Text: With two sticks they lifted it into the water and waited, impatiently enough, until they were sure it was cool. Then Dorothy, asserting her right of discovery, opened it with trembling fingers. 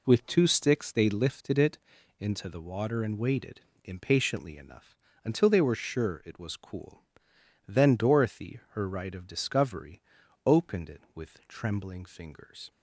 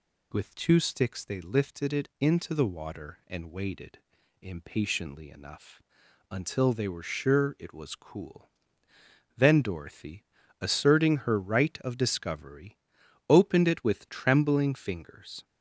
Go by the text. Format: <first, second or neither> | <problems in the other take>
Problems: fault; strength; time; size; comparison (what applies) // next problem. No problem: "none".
second | pauses between "it" and "into"; at 1.7 s; 0.40 s long // skips "asserting"; at 8.6 s